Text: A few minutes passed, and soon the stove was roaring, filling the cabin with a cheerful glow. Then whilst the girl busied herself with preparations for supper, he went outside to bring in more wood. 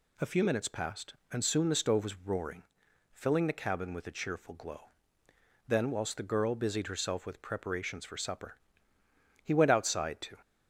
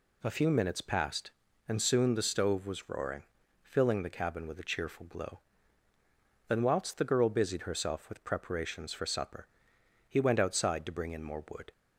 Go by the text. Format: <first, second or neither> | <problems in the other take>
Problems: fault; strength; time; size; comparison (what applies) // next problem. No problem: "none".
second | stops before "bring in more wood"; at 10.4 s